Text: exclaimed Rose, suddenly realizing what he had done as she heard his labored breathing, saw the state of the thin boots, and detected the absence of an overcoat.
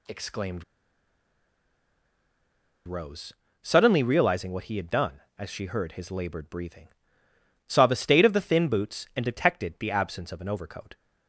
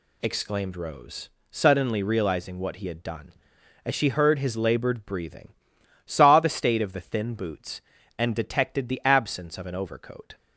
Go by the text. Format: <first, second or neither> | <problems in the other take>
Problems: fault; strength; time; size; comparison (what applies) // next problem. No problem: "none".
second | pauses between "exclaimed" and "Rose"; strong; at 0.6 s; 2.2 s long